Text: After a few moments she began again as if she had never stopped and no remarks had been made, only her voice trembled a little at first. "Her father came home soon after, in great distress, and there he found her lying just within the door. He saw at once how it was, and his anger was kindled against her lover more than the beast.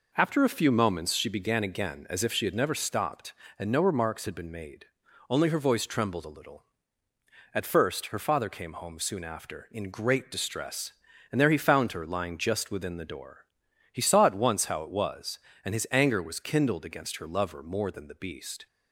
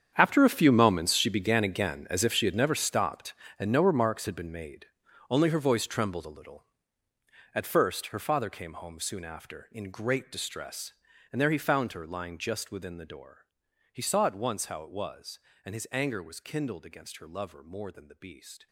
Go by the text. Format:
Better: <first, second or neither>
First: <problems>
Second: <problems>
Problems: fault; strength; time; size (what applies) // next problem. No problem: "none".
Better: first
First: none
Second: gets quieter; strong; throughout; 16.5 dB